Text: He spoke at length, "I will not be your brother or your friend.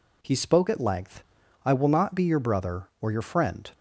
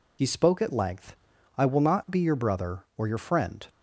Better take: first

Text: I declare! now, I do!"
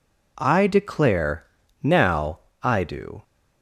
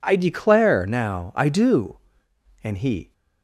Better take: first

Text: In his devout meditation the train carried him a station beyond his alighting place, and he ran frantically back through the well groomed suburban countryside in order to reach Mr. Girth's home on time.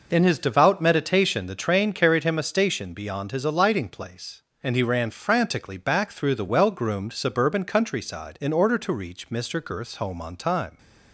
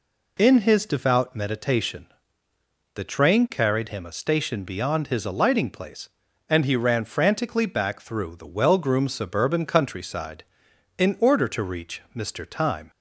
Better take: first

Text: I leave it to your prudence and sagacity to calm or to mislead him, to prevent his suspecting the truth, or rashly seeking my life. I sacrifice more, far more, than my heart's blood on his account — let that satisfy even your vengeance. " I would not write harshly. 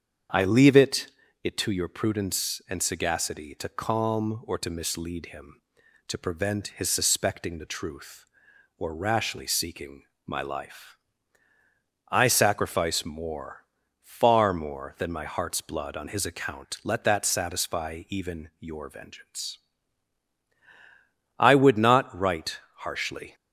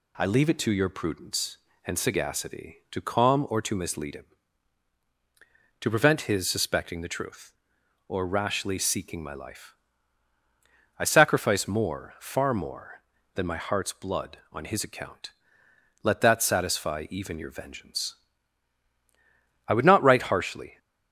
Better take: second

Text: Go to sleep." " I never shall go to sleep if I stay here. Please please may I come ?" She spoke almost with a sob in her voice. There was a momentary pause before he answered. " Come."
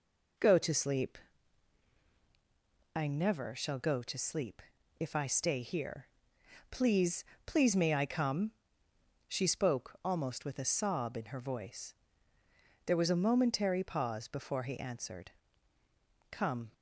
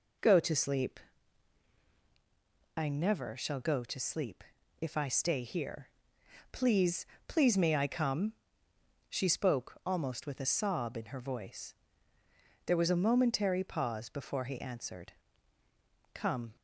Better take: neither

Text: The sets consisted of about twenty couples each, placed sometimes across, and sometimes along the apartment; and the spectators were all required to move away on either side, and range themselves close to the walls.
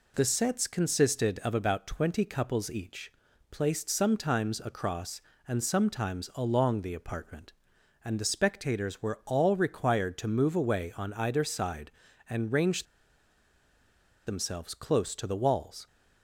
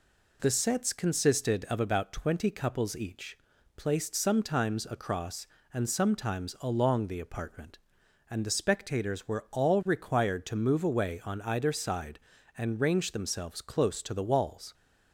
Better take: second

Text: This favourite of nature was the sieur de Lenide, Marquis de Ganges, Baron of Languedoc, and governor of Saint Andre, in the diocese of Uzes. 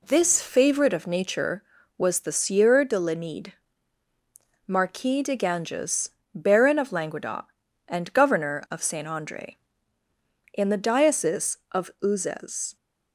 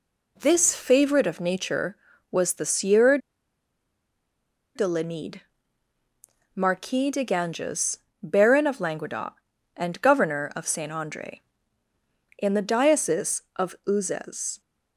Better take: first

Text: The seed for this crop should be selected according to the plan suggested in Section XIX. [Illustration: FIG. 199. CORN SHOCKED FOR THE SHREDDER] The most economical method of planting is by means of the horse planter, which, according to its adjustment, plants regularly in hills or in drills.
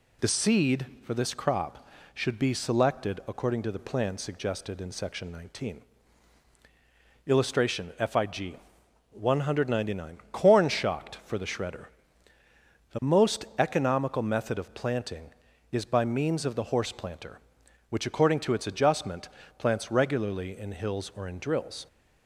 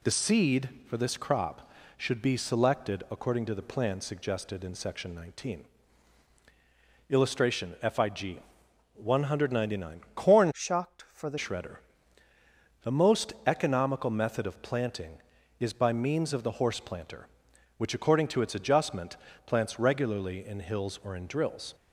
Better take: first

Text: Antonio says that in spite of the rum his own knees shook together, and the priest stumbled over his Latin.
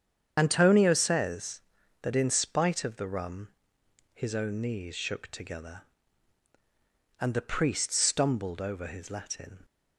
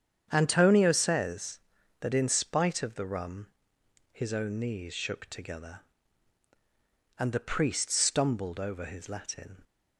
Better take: second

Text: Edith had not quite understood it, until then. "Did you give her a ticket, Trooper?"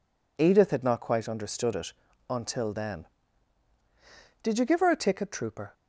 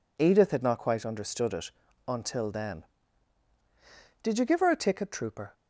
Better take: neither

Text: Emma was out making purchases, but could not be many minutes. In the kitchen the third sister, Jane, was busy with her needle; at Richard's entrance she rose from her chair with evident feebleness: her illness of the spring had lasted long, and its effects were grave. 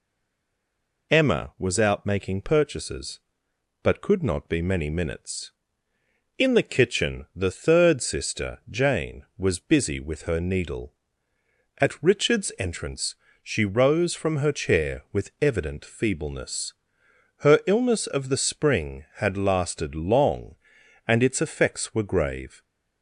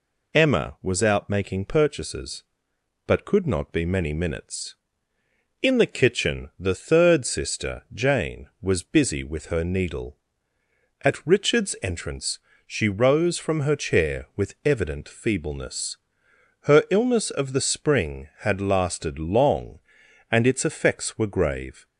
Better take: second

